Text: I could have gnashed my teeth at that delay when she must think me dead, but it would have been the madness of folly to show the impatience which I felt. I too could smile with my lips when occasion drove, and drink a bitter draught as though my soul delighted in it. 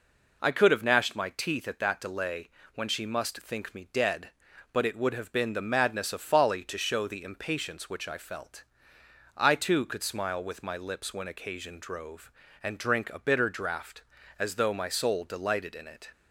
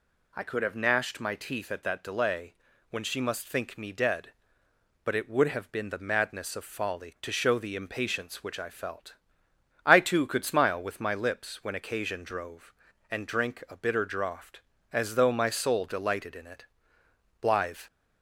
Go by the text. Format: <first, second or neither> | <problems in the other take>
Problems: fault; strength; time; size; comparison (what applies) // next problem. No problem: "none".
first | pauses between "delay" and "when"; slight; at 2.5 s; 0.36 s long; slight in the first // goes on to say "Blithe"; slight; from 17.4 s on; 0.38 s long